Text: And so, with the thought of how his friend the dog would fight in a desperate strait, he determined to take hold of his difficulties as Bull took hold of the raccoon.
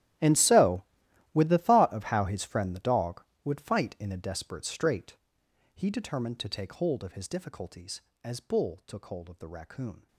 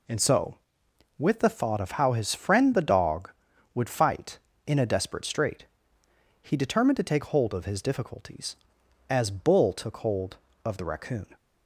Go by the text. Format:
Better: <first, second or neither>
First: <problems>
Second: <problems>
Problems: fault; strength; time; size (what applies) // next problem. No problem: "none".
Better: second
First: gets quieter; strong; throughout; 20 dB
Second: none